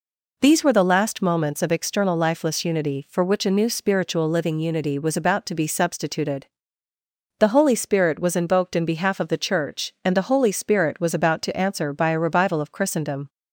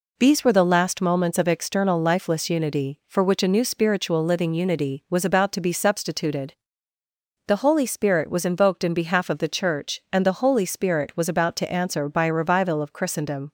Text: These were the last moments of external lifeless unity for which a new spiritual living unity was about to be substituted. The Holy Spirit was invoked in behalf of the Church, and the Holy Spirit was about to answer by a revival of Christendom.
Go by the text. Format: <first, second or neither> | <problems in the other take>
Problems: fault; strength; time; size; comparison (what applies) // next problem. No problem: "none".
neither | none